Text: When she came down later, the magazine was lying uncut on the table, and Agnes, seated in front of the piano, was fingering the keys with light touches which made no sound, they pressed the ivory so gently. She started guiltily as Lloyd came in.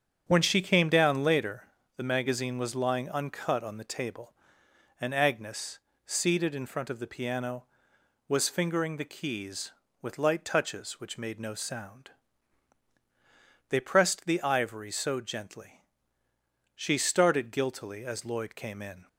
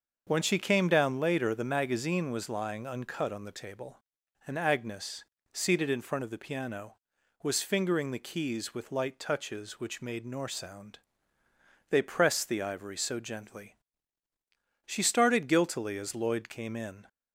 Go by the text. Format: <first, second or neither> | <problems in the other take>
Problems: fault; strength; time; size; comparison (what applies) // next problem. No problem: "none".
first | starts louder than the rest; until 1.2 s; 6.5 dB; strong in the first // says "nor" for "no"; at 10.2 s